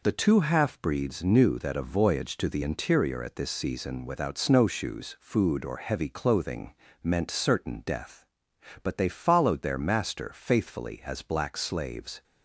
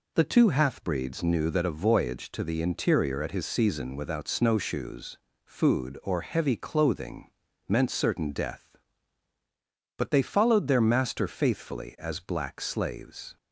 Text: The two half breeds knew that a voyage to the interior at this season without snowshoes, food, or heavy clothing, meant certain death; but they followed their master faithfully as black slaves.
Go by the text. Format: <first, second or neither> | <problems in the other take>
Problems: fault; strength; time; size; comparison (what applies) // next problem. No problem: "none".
first | says "his" for "this"; at 3.3 s